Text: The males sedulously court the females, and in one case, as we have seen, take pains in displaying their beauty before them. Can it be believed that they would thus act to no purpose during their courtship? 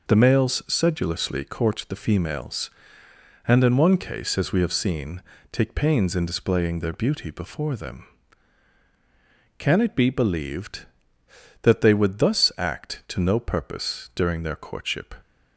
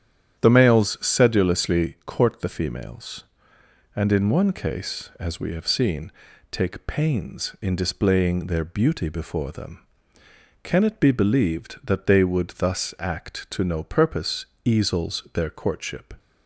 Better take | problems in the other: first | starts louder than the rest; strong; until 1.4 s; 9.5 dB // says "easels" for "during"; at 14.6 s

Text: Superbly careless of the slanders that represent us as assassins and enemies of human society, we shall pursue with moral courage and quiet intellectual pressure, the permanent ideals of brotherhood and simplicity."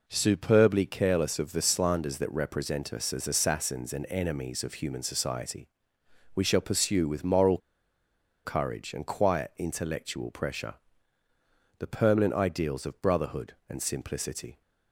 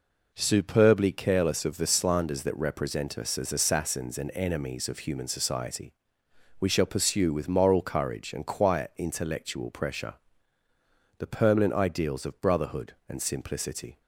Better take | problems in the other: second | pauses between "moral" and "courage"; noticeable; at 7.5 s; 0.86 s long

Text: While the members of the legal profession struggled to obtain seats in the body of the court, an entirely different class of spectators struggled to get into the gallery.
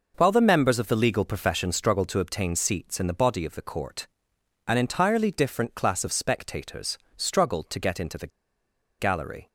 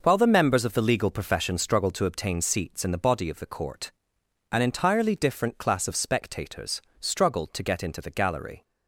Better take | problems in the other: second | pauses between "spectators" and "struggled"; slight; at 6.9 s; 0.20 s long; slight in the second // pauses between "the" and "gallery"; noticeable; at 8.2 s; 0.71 s long

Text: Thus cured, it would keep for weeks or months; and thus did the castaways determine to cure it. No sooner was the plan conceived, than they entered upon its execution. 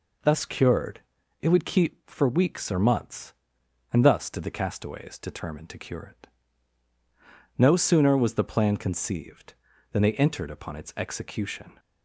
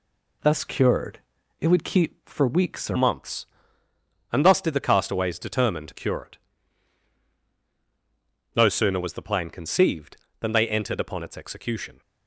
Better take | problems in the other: first | changes voice at "months"; from 2.9 s on; 9.1 s long

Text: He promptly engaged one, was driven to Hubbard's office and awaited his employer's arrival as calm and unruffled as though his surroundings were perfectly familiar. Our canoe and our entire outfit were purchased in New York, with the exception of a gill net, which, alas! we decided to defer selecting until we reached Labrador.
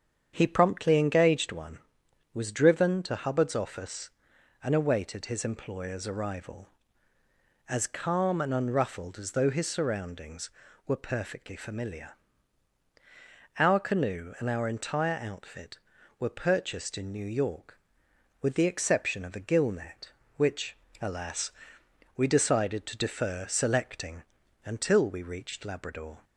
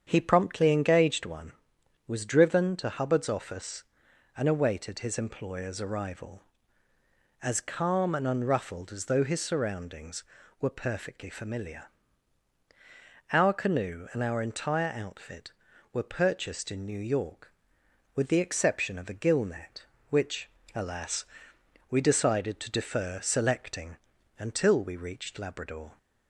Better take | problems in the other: neither | starts louder than the rest; strong; the same in both // pauses between "selecting" and "until"; the same in both

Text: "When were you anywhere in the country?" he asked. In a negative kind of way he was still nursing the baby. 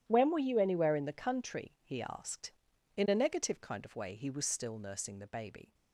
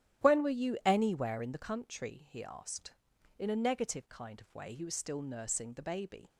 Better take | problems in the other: second | gets quieter; strong; throughout; 14.5 dB // starts louder than the rest; strong; until 1.0 s; 10.5 dB; strong in the second

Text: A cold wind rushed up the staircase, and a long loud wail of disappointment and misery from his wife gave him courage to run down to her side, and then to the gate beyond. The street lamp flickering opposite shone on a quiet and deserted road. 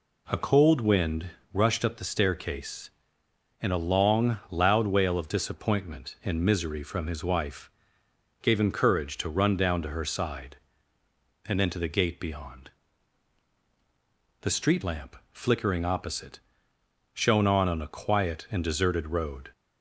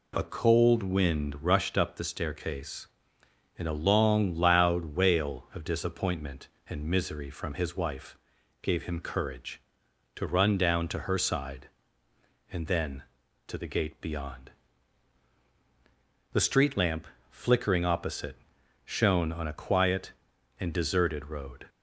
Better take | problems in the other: second | pauses between "wind" and "rushed"; slight; at 1.2 s; 0.24 s long // pauses between "wife" and "gave"; noticeable; at 7.7 s; 0.70 s long; noticeable in the second // pauses between "lamp" and "flickering"; slight; at 15.1 s; 0.18 s long; slight in the second // pauses between "opposite" and "shone"; noticeable; at 16.3 s; 0.76 s long; noticeable in the second // says "on" twice; at 17.6 s

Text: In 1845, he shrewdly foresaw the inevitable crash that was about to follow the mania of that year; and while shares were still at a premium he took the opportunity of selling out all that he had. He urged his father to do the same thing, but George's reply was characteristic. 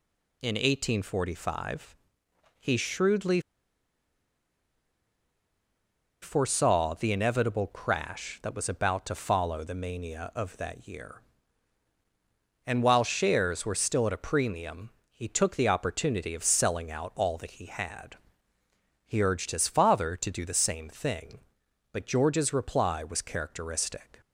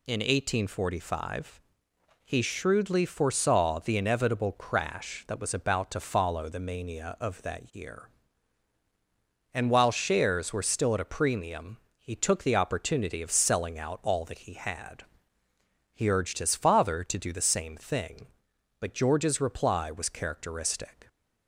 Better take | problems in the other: second | pauses between "shrewdly" and "foresaw"; strong; at 3.4 s; 2.8 s long // pauses between "premium" and "he"; slight; at 14.9 s; 0.18 s long; slight in the second

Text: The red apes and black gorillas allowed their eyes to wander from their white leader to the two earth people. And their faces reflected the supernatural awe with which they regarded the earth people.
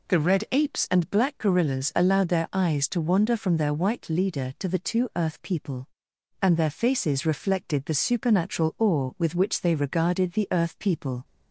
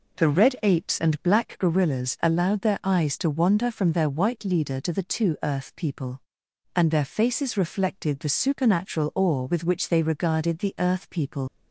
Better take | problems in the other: first | leaves "people" unfinished; at 11.4 s; 90 ms

